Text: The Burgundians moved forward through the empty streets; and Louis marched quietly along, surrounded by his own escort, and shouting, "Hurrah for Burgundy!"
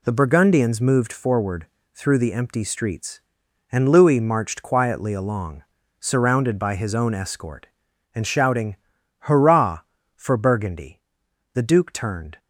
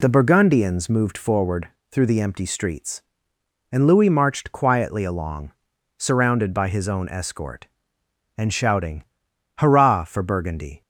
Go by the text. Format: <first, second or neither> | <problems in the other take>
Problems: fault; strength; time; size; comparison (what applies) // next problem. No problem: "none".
second | pauses between "forward" and "through"; slight; at 1.6 s; 0.28 s long; slight in the second // goes on to say "The duke turned"; noticeable; from 11.5 s on; 0.86 s long